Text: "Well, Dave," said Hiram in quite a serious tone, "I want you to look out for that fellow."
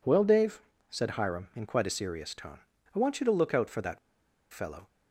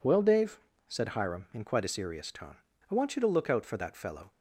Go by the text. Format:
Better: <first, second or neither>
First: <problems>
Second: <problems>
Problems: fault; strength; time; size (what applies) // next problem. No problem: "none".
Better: second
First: pauses between "that" and "fellow"; noticeable; at 3.9 s; 0.54 s long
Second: none